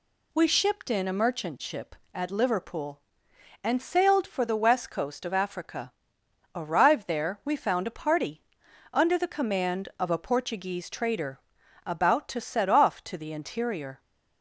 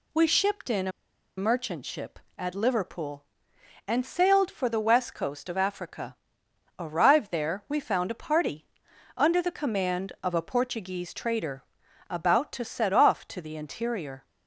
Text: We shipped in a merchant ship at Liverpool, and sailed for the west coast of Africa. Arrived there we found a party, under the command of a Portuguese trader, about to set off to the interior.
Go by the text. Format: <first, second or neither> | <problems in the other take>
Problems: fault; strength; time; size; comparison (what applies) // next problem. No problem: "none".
first | pauses between "a" and "merchant"; noticeable; at 0.9 s; 0.47 s long